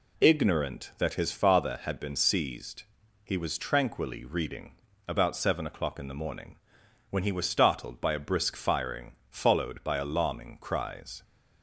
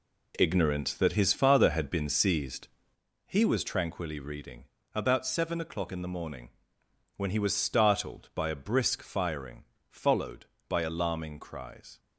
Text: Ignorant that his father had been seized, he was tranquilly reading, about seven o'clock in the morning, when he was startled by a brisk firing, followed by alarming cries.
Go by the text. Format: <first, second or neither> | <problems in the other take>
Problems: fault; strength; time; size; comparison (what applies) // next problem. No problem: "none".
first | gets quieter; strong; throughout; 9 dB